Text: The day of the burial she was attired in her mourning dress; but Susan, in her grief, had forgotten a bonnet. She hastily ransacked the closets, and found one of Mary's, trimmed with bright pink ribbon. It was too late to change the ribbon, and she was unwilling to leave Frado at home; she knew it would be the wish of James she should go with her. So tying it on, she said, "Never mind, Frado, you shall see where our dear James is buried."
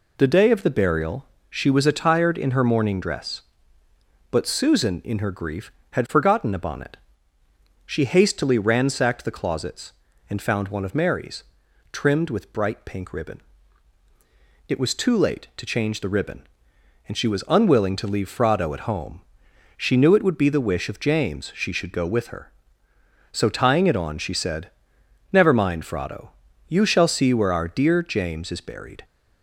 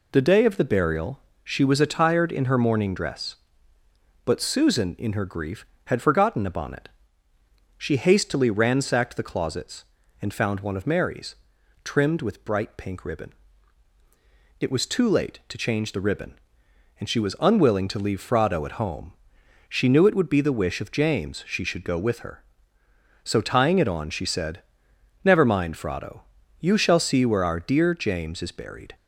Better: neither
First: pauses between "burial" and "she"; slight; at 1.2 s; 0.24 s long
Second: pauses between "burial" and "she"; slight; at 1.1 s; 0.24 s long

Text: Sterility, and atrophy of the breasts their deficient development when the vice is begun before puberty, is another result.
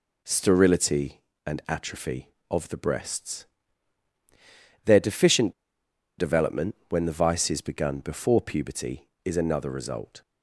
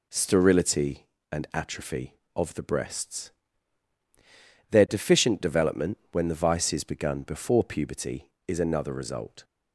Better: second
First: pauses between "breasts" and "their"; strong; at 3.4 s; 1.4 s long // pauses between "deficient" and "development"; noticeable; at 5.5 s; 0.65 s long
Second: pauses between "breasts" and "their"; strong; at 3.3 s; 1.4 s long

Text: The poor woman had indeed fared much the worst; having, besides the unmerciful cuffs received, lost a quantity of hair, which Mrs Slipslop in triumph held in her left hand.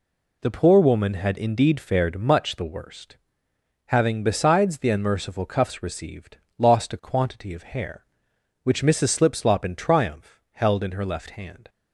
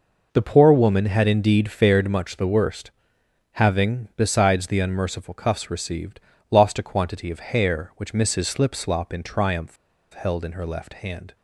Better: first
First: none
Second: pauses between "triumph" and "held"; at 9.7 s; 0.37 s long

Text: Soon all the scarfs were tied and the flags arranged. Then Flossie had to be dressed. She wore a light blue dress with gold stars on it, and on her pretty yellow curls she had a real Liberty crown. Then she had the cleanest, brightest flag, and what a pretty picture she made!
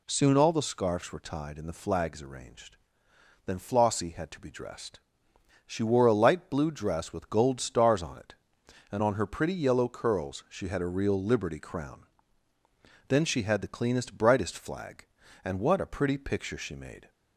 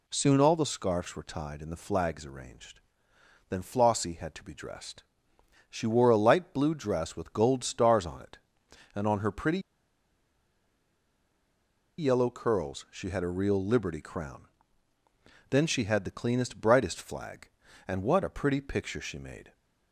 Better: first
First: none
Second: pauses between "pretty" and "yellow"; strong; at 9.5 s; 2.3 s long

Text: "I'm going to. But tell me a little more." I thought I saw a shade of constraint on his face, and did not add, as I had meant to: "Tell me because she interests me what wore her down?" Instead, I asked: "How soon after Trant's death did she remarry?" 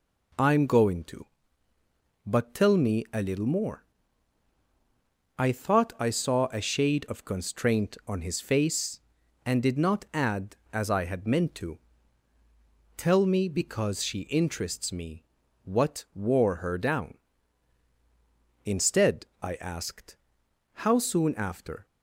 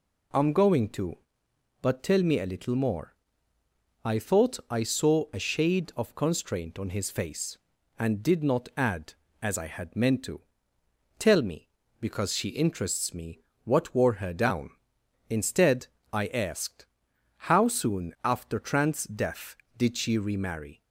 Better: second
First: pauses between "me" and "what"; at 15.2 s; 0.42 s long // stops before "Trant's death did she remarry"; at 21.8 s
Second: pauses between "me" and "what"; slight; at 13.3 s; 0.26 s long

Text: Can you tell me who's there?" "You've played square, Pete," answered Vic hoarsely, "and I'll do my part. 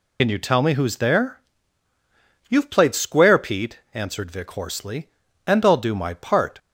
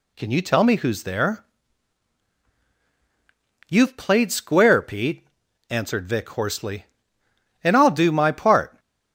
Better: second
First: loses the start of "Can"; at 0.1 s; 60 ms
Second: none

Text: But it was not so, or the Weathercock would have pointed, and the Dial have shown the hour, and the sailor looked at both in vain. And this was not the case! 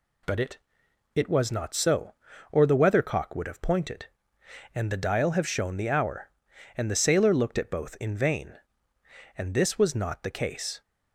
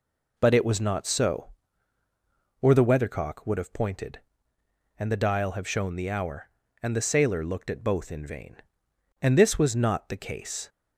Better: second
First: says "it" twice; at 1.1 s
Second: none

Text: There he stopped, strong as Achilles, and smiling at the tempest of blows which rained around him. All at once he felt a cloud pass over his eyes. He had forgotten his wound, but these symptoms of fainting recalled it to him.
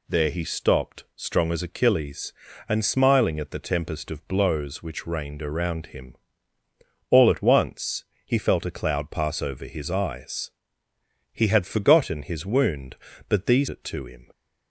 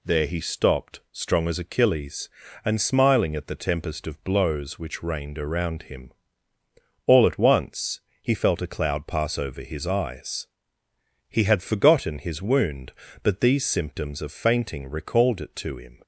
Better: second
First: pauses between "once" and "he"; slight; at 8.0 s; 0.22 s long // skips "symptoms of fainting recalled"; at 13.6 s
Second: pauses between "once" and "he"; slight; at 7.9 s; 0.22 s long

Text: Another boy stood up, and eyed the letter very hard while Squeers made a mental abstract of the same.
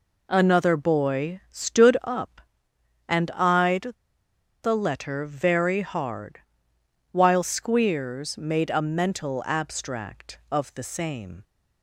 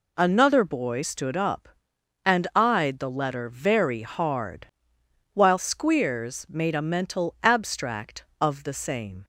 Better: second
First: pauses between "eyed" and "the"; noticeable; at 3.9 s; 0.71 s long // pauses between "hard" and "while"; noticeable; at 6.3 s; 0.74 s long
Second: pauses between "hard" and "while"; noticeable; at 4.6 s; 0.66 s long

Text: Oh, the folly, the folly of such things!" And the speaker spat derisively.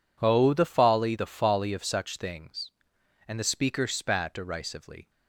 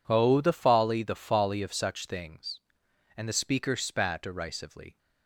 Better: neither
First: none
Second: none

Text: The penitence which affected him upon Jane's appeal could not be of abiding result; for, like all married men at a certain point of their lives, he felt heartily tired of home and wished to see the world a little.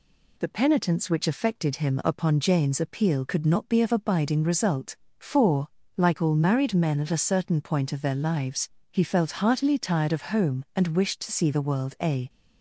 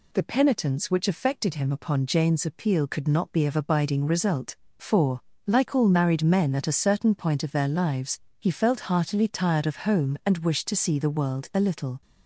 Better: second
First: stops before "little"; at 12.2 s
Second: none

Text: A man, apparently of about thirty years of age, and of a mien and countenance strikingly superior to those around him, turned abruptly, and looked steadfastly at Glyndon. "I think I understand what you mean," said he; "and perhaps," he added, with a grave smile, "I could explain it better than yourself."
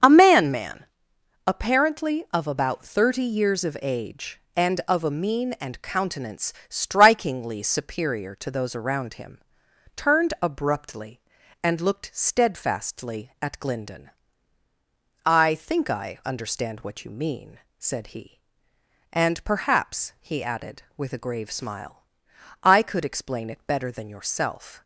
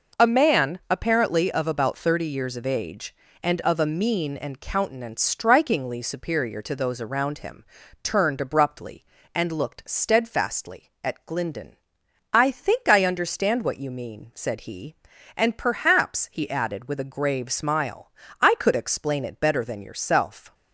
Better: second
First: starts louder than the rest; until 1.6 s; 7 dB // says "man" twice; at 0.5 s // pauses between "countenance" and "strikingly"; slight; at 6.5 s; 0.16 s long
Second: none

